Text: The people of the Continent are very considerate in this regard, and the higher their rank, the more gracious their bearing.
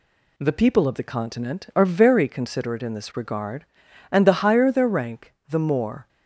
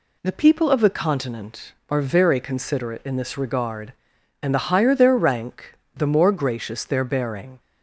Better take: second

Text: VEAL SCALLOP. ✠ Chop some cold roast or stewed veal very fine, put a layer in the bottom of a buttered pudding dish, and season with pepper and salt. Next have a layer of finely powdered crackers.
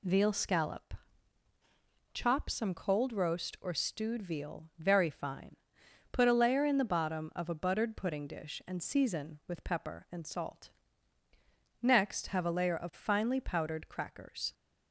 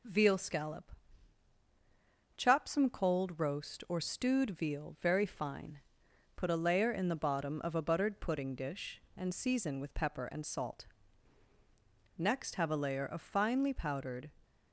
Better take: first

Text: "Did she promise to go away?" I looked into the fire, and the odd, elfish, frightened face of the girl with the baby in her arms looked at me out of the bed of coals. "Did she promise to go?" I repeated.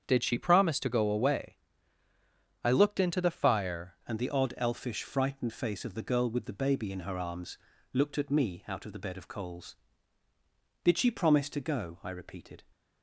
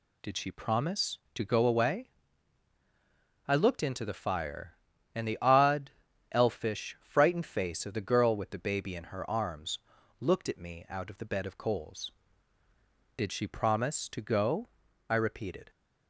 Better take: second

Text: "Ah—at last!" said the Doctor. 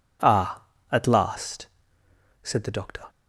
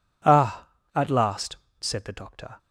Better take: neither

